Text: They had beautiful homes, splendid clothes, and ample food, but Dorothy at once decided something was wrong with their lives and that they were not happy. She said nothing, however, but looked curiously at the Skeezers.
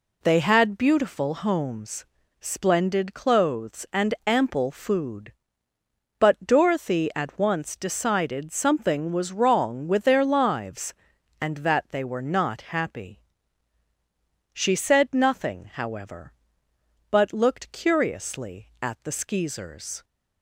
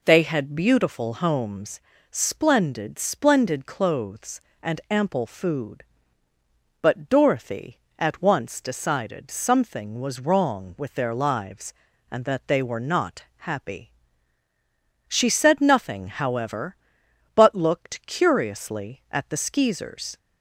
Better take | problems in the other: first | says "splendid" twice; at 2.9 s // pauses between "not" and "happy"; slight; at 13.2 s; 0.16 s long

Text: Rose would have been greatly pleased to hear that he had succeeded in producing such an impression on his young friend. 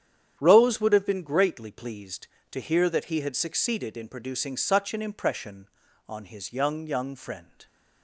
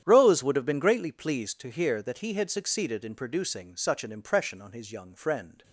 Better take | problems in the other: second | starts louder than the rest; strong; until 1.4 s; 9 dB; strong in the second // says "young" twice; at 6.8 s

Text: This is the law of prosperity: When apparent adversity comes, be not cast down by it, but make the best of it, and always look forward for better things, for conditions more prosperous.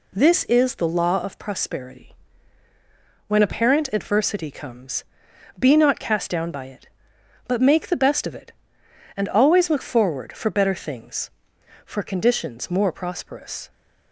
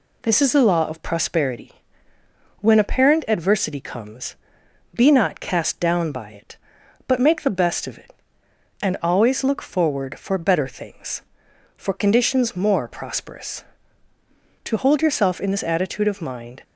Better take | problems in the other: first | goes on to say "To hold yourself in this attitude of mind"; strong; from 14.6 s on; 1.9 s long

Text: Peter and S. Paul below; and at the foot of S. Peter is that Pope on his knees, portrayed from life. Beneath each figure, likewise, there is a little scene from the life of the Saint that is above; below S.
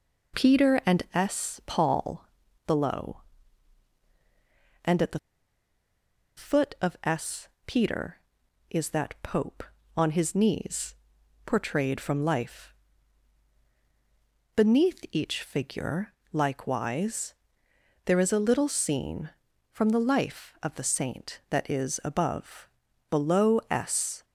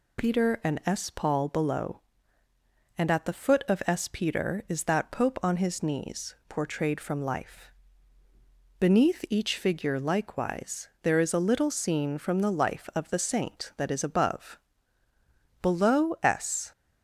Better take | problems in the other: second | pauses between "Paul" and "below"; at 2.2 s; 0.40 s long // pauses between "the" and "foot"; at 5.1 s; 1.1 s long

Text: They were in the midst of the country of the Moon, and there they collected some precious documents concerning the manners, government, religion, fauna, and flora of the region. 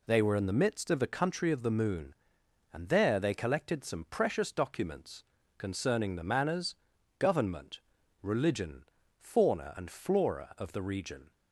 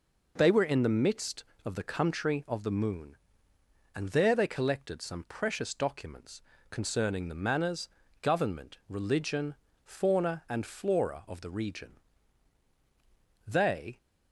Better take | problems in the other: first | pauses between "documents" and "concerning"; slight; at 6.4 s; 0.26 s long; slight in the first // goes on to say "They"; from 13.4 s on; 0.52 s long

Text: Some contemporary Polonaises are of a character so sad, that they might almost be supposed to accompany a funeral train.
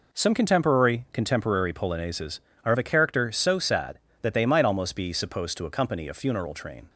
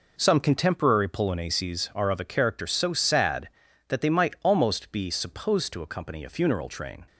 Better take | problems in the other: second | says "contemporary" twice; at 1.1 s

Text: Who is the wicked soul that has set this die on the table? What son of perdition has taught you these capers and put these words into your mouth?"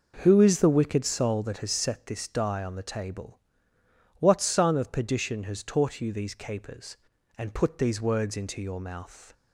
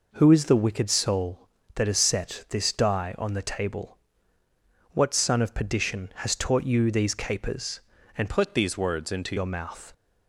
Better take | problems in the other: first | changes voice from "put" to "into"; from 8.2 to 9.3 s; 1.1 s long

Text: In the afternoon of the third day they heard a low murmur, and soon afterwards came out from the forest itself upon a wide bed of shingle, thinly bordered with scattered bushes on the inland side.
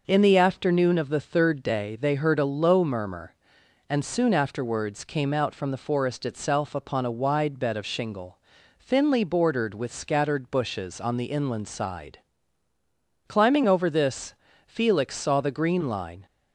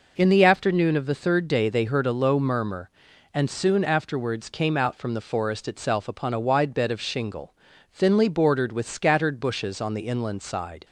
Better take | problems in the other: second | goes on to say "Climbing over this Felix saw the green line"; strong; from 13.2 s on; 2.9 s long

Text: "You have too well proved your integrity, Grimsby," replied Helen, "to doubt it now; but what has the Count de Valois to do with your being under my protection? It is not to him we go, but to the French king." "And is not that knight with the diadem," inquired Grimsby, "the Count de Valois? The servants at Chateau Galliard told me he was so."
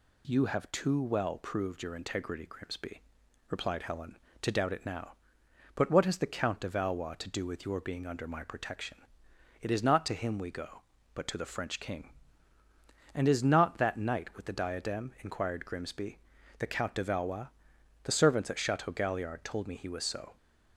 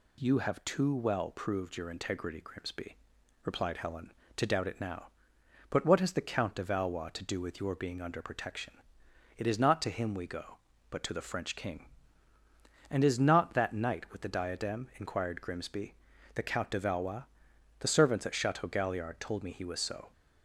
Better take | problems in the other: first | skips "my"; at 8.2 s

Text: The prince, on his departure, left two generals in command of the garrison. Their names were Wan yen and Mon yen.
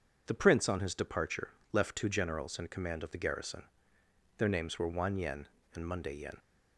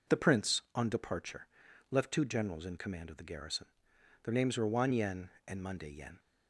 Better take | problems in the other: first | skips "his"; at 0.8 s

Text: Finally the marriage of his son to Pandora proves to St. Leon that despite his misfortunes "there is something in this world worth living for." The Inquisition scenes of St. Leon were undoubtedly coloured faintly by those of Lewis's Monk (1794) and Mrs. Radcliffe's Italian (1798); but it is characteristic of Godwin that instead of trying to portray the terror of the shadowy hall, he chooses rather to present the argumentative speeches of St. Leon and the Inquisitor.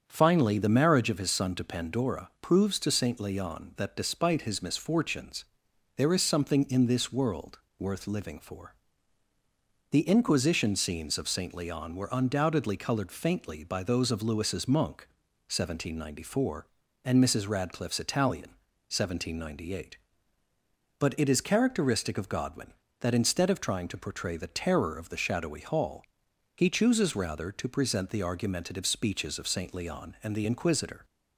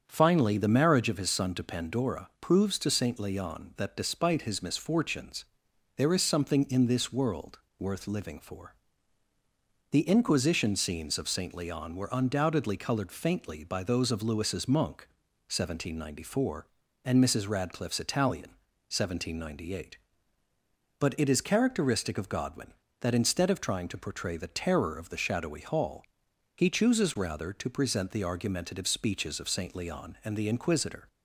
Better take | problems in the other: neither | starts louder than the rest; strong; the same in both // pauses between "misfortunes" and "there"; noticeable; the same in both // pauses between "world" and "worth"; slight; the same in both

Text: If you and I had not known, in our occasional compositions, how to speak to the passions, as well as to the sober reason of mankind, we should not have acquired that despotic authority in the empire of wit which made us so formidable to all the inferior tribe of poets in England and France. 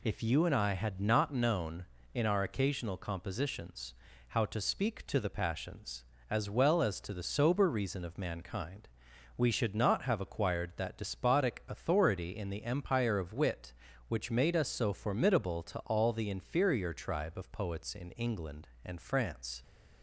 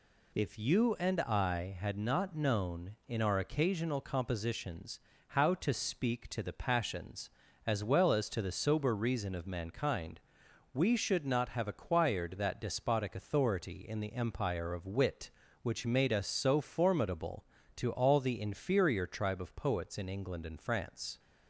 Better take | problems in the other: neither | none

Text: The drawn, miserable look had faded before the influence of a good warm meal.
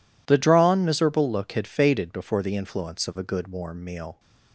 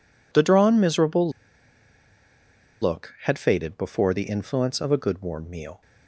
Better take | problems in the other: first | pauses between "miserable" and "look"; strong; at 1.2 s; 1.5 s long

